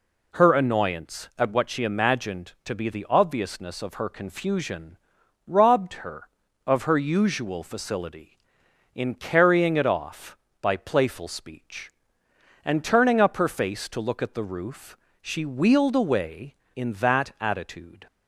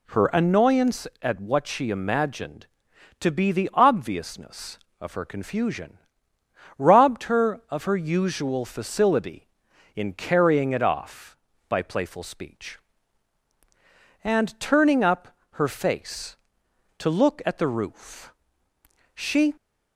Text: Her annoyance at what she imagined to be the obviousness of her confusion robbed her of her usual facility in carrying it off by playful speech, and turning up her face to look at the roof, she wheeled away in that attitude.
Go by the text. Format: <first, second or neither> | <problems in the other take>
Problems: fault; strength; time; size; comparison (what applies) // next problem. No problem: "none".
first | pauses between "confusion" and "robbed"; noticeable; at 5.9 s; 0.78 s long; noticeable in the first // pauses between "up" and "her"; slight; at 15.2 s; 0.22 s long // stops before "wheeled away in that attitude"; at 19.5 s